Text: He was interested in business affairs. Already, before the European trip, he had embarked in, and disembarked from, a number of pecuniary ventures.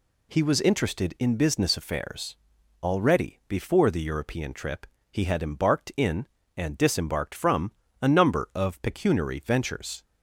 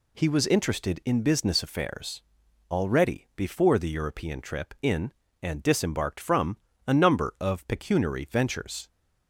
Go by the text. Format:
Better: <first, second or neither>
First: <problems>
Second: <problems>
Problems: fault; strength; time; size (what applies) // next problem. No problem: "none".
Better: first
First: none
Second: skips "he had embarked"; at 4.7 s